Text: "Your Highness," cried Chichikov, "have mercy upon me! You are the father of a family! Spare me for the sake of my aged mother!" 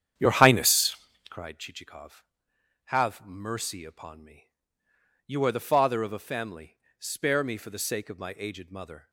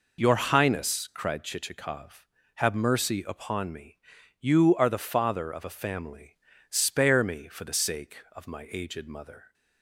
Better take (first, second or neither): second